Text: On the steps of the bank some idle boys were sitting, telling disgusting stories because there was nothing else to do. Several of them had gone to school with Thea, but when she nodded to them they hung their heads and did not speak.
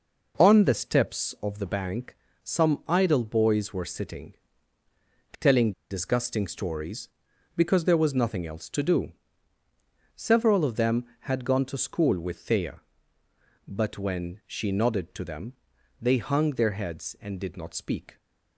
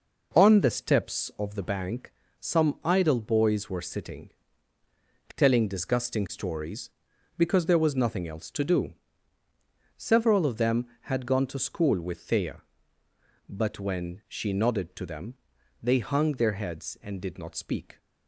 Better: second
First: pauses between "bank" and "some"; slight; at 2.1 s; 0.30 s long // pauses between "telling" and "disgusting"; slight; at 5.7 s; 0.18 s long // pauses between "them" and "they"; noticeable; at 15.5 s; 0.48 s long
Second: pauses between "bank" and "some"; slight; at 2.1 s; 0.30 s long // pauses between "them" and "they"; noticeable; at 15.3 s; 0.48 s long

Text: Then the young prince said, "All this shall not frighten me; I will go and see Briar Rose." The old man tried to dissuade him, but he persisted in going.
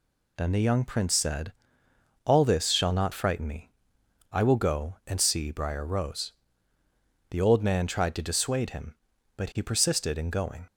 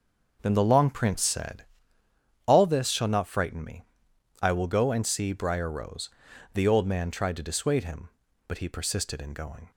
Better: first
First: none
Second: says "long" for "young"; at 0.6 s

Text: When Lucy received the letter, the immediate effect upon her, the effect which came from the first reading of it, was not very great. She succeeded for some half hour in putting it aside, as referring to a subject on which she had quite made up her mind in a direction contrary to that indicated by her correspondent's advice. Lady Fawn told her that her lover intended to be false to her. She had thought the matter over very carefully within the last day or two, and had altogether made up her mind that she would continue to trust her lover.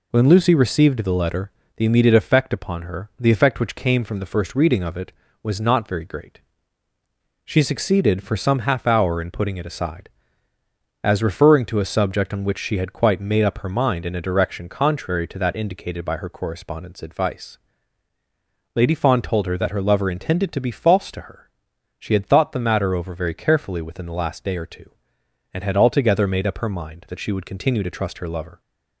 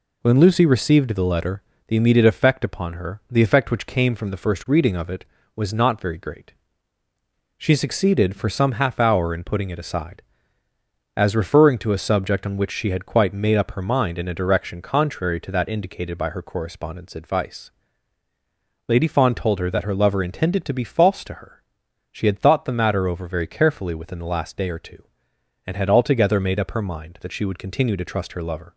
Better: neither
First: none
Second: none

